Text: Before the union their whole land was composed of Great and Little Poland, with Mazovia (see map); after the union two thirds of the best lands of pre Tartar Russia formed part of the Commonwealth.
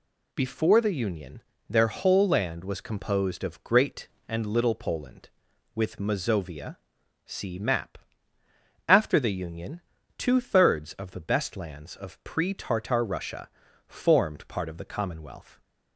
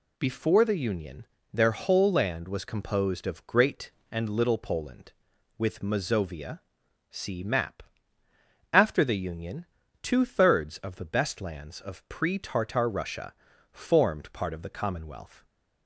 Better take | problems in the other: neither | pauses between "union" and "their"; slight; the same in both // pauses between "union" and "two"; the same in both // pauses between "Russia" and "formed"; the same in both

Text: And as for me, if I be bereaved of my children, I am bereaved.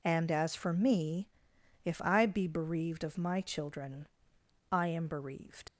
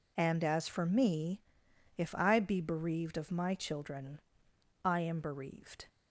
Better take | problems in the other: second | leaves "bereaved" unfinished; at 5.6 s; 75 ms

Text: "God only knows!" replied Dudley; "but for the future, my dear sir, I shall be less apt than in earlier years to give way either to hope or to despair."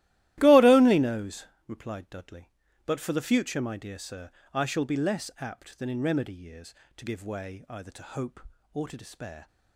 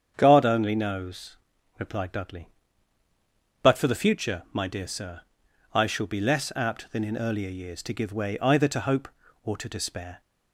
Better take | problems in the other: second | starts louder than the rest; strong; until 1.3 s; 15.5 dB; strong in the second // says "remedy" for "earlier"; at 6.0 s

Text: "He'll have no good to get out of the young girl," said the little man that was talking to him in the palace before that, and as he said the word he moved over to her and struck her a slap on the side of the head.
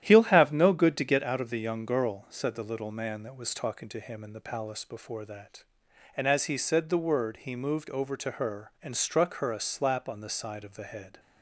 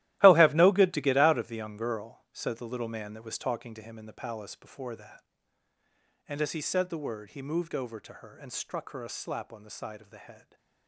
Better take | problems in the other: first | gets quieter; strong; throughout; 13 dB // starts louder than the rest; strong; until 1.2 s; 15 dB; strong in the first

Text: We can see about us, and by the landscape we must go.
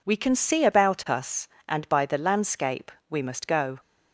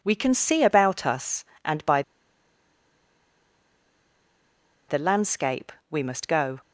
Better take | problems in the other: first | pauses between "by" and "the"; strong; at 2.0 s; 2.8 s long // pauses between "landscape" and "we"; slight; at 5.7 s; 0.18 s long; slight in the first

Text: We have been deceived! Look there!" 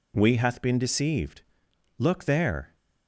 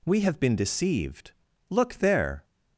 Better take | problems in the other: second | says "hath" for "have"; at 0.3 s

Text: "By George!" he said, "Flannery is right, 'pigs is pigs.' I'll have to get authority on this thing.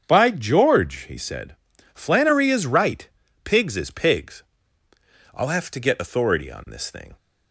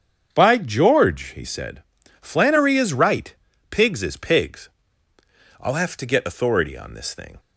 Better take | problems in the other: neither | starts louder than the rest; strong; the same in both

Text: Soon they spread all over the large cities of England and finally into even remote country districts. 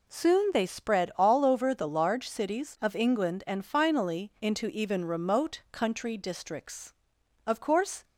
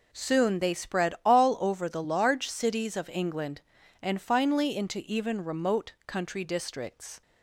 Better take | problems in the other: second | goes on to say "Of course"; from 7.4 s on; 0.58 s long

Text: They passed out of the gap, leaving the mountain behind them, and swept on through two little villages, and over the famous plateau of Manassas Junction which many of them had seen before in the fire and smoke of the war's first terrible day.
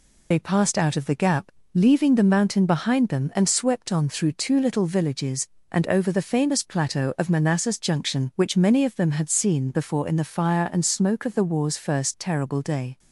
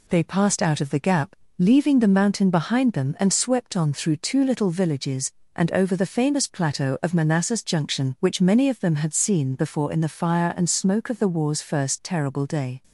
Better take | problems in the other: second | loses the start of "They"; at 0.3 s; 60 ms

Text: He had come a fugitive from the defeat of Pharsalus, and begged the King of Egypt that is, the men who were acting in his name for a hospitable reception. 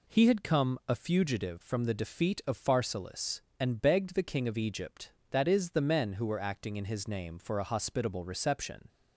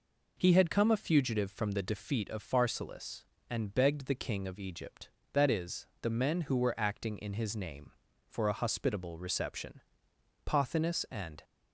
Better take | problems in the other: first | goes on to say "Pothinus and"; noticeable; from 10.4 s on; 0.96 s long

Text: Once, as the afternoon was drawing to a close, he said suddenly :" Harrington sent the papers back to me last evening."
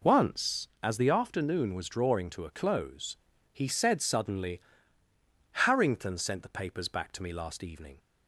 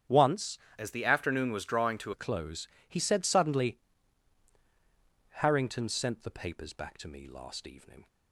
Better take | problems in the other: first | starts louder than the rest; strong; until 1.3 s; 10 dB // changes voice from "as" to "to"; from 0.7 to 2.1 s; 1.4 s long

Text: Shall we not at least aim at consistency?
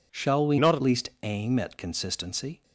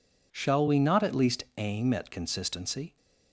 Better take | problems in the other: second | changes voice from "not" to "at"; from 0.5 to 0.8 s; 0.3 s long

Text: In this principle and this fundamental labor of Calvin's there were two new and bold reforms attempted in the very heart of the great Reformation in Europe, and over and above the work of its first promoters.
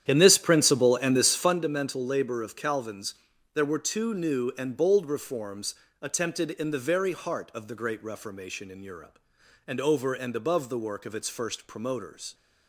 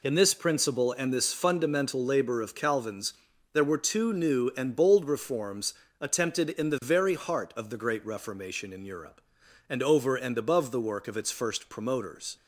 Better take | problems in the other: second | starts louder than the rest; strong; until 1.6 s; 10 dB // pauses between "Calvin's" and "there"; at 3.1 s; 0.40 s long; also in the second // pauses between "reforms" and "attempted"; slight; at 5.7 s; 0.26 s long; slight in the second

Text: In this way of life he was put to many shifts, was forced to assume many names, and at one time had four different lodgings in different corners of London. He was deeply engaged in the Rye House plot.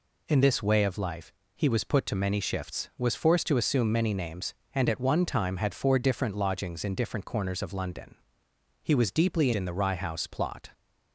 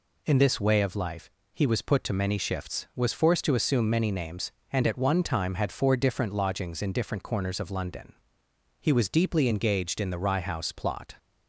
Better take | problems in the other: second | pauses between "life" and "he"; slight; at 1.3 s; 0.24 s long; slight in the second // skips "engaged"; at 9.5 s

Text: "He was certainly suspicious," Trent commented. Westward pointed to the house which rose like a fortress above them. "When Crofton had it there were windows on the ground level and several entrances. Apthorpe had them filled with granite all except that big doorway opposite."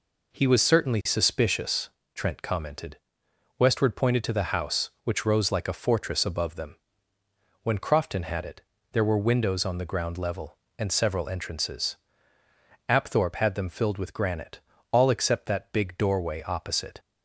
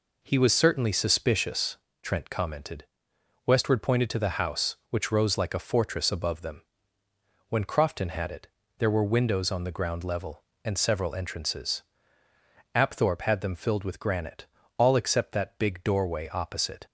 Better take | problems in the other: neither | pauses between "it" and "there"; slight; the same in both // pauses between "granite" and "all"; slight; the same in both

